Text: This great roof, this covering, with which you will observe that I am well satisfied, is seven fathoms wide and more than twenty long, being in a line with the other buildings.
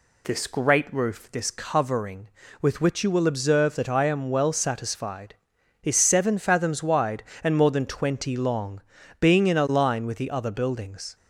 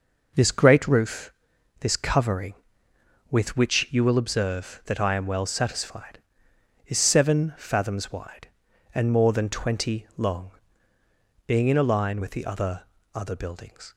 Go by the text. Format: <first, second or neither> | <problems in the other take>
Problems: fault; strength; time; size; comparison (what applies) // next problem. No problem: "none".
first | says "other" twice; at 13.1 s